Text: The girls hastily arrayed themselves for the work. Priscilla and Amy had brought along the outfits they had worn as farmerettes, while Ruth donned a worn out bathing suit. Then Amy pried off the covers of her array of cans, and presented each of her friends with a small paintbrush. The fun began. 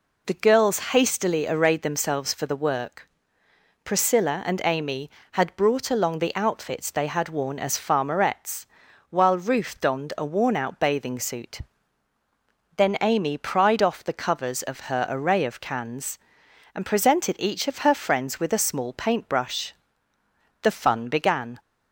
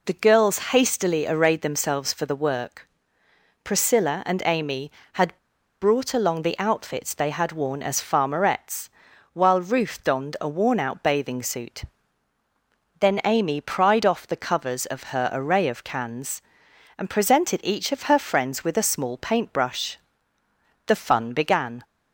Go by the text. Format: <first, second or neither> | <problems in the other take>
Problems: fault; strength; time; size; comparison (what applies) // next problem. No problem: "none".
first | pauses between "had" and "brought"; at 5.3 s; 0.45 s long